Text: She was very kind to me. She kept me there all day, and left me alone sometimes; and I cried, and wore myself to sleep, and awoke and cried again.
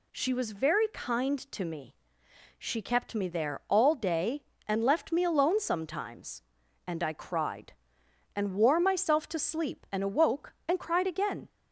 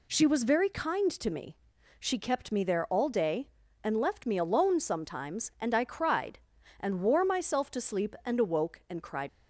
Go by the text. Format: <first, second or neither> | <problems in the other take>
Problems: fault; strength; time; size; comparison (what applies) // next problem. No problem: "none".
first | stops before "again"; at 9.2 s